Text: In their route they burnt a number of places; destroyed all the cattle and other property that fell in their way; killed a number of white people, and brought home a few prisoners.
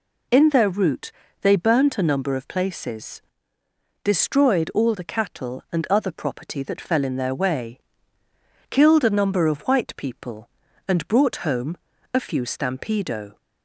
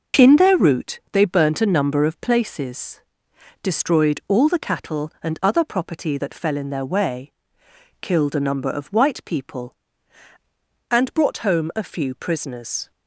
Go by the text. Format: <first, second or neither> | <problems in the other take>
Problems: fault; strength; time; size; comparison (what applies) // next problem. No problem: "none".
second | pauses between "route" and "they"; slight; at 1.1 s; 0.30 s long // pauses between "home" and "a"; slight; at 11.7 s; 0.36 s long // says "stampedo" for "prisoners"; at 12.4 s